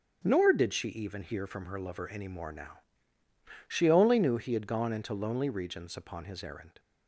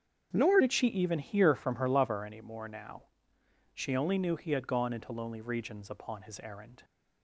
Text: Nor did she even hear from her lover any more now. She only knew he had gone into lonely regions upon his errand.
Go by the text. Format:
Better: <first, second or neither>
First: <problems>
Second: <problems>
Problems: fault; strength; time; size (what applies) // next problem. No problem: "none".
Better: first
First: starts louder than the rest; strong; until 1.2 s; 7 dB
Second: starts louder than the rest; strong; until 1.3 s; 8 dB // changes voice at "did"; from 0.6 s on; 6.2 s long